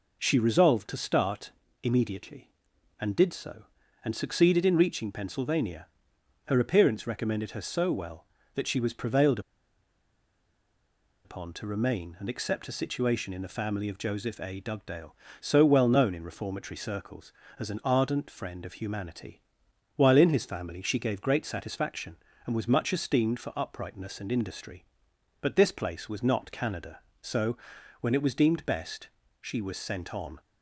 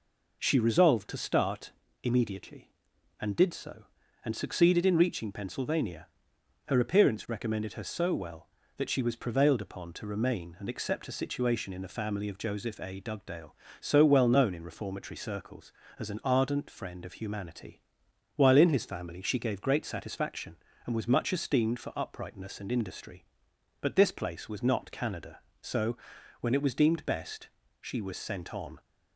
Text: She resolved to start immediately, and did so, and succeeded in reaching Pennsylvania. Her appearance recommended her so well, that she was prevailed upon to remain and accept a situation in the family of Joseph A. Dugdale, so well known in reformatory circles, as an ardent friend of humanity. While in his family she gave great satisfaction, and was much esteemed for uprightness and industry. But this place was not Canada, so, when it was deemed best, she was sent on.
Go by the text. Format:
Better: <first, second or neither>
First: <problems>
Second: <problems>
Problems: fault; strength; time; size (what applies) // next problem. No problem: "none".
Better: second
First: pauses between "start" and "immediately"; slight; at 1.5 s; 0.30 s long // pauses between "prevailed" and "upon"; strong; at 9.3 s; 1.8 s long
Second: pauses between "start" and "immediately"; slight; at 1.7 s; 0.30 s long